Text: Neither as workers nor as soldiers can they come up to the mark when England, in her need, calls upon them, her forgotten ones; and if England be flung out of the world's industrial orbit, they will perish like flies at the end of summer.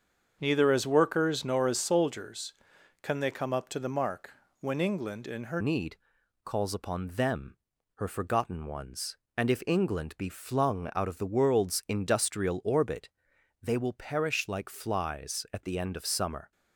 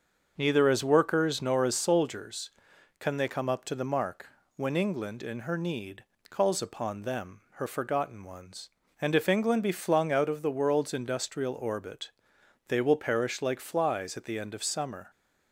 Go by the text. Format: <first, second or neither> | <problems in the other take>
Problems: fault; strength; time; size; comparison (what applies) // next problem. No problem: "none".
second | starts louder than the rest; until 1.4 s; 7 dB; also in the second // pauses between "mark" and "when"; slight; at 4.3 s; 0.28 s long; slight in the second // changes voice at "need"; from 5.6 s on; 10.9 s long